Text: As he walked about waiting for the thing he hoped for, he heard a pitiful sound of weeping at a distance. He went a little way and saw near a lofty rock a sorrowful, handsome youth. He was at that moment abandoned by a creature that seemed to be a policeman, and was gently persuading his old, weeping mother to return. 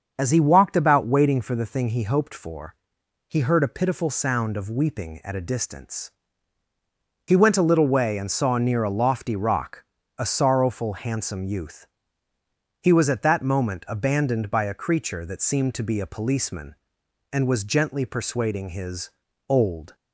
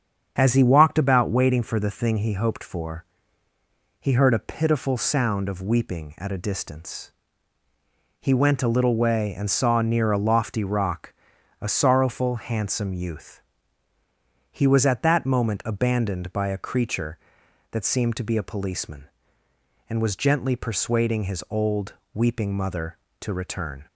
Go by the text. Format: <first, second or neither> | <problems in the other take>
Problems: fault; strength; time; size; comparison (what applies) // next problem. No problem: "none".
second | starts louder than the rest; until 1.1 s; 6.5 dB; strong in the second // pauses between "rock" and "a"; slight; at 9.8 s; 0.34 s long; also in the second // pauses between "his" and "old"; at 19.0 s; 0.40 s long // stops before "weeping mother to return"; at 19.9 s